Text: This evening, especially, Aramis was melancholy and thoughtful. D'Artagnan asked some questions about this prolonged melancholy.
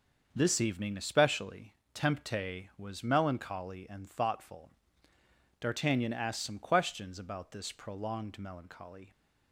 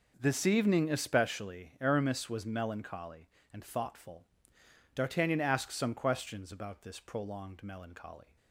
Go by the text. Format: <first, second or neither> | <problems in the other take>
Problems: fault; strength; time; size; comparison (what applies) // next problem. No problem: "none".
second | starts louder than the rest; until 1.3 s; 6.5 dB // says "Tempte" for "Aramis"; at 1.9 s